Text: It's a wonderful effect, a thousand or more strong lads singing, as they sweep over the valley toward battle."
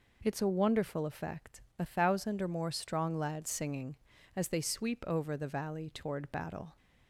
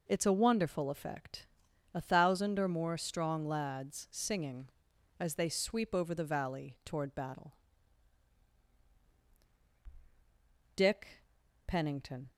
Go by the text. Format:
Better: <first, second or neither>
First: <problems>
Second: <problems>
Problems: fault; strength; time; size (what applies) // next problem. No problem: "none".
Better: first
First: none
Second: goes on to say "Dick Pennington"; from 10.7 s on; 1.5 s long